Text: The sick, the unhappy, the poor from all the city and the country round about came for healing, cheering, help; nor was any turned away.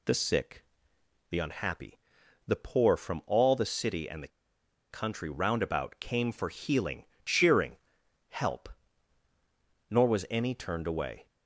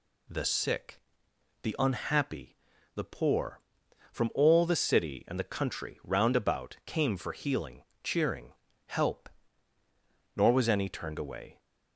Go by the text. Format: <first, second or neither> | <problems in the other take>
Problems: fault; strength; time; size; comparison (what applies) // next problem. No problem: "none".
second | pauses between "the" and "country"; noticeable; at 4.2 s; 0.63 s long